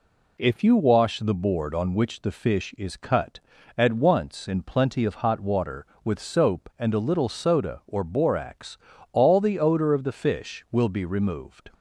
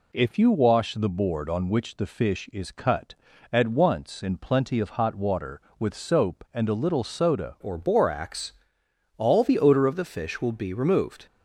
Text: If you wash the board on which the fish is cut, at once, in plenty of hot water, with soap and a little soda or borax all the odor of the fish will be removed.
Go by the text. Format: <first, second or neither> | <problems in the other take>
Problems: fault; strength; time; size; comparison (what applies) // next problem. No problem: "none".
first | changes voice at "or"; from 7.6 s on; 3.6 s long // pauses between "borax" and "all"; noticeable; at 8.5 s; 0.64 s long; slight in the first